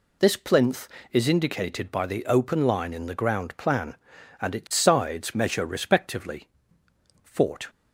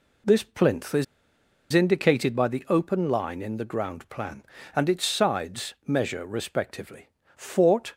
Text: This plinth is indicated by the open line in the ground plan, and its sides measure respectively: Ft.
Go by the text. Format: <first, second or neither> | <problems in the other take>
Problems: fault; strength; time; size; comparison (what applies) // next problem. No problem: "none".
first | pauses between "is" and "indicated"; noticeable; at 1.0 s; 0.67 s long